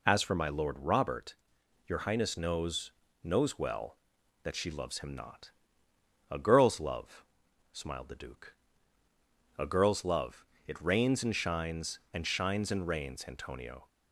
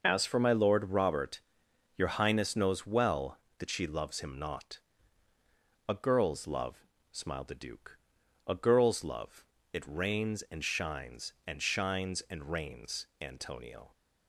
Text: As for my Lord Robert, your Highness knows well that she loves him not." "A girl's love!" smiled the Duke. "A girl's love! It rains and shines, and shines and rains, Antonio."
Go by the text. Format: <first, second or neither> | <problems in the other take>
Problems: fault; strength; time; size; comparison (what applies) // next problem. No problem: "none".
second | says "knows" twice; at 3.2 s